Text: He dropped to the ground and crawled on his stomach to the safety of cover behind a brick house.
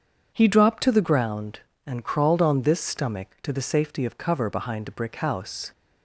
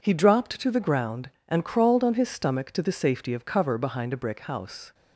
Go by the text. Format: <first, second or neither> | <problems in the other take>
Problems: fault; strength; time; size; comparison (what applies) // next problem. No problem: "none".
second | starts louder than the rest; until 1.3 s; 7 dB // says "this" for "his"; at 2.6 s